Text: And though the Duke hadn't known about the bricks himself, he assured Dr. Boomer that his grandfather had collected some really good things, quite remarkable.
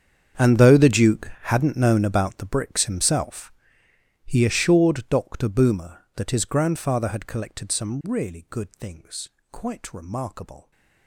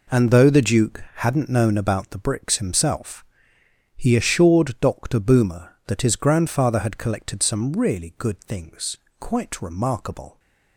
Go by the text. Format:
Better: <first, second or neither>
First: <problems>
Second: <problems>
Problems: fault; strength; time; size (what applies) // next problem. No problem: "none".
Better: second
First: gets quieter; strong; throughout; 19.5 dB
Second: none